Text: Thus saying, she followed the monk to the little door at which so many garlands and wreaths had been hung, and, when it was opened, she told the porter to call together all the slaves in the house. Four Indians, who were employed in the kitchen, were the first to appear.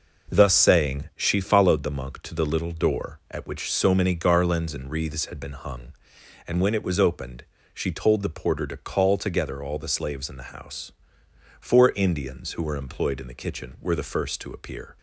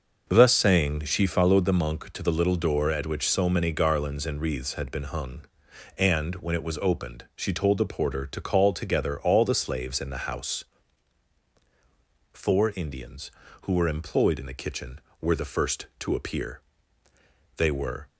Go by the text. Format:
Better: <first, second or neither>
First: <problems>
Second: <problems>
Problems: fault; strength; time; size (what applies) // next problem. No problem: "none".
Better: first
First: none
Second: goes on to say "They were"; from 17.5 s on; 0.52 s long